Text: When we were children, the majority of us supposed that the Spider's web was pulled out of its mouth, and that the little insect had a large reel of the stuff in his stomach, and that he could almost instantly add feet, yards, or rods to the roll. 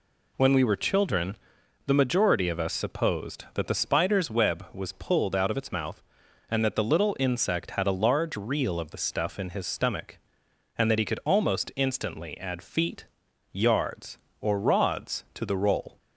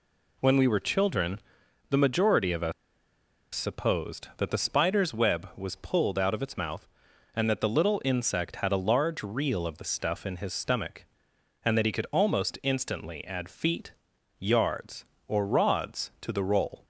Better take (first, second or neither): first